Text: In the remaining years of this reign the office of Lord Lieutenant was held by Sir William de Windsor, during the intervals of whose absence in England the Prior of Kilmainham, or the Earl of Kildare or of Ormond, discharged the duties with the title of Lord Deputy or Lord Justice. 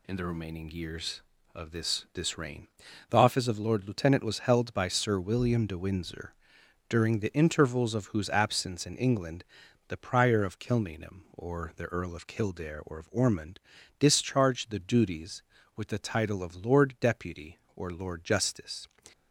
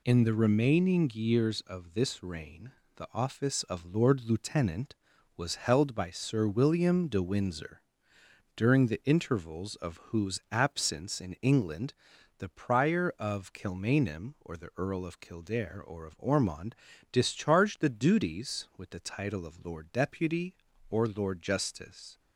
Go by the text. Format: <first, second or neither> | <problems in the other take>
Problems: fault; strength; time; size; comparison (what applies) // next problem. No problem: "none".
second | says "this" twice; at 2.1 s // pauses between "reign" and "the"; at 2.6 s; 0.42 s long; slight in the second // pauses between "England" and "the"; at 9.4 s; 0.44 s long; also in the second